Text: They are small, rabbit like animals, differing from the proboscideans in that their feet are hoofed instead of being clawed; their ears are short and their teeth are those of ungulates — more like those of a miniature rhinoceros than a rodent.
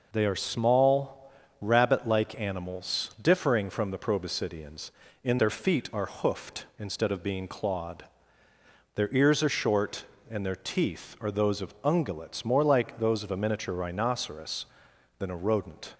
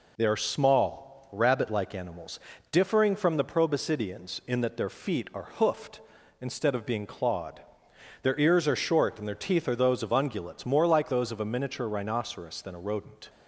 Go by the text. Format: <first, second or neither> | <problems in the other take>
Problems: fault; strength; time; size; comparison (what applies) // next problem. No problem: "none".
second | skips "that"; at 5.3 s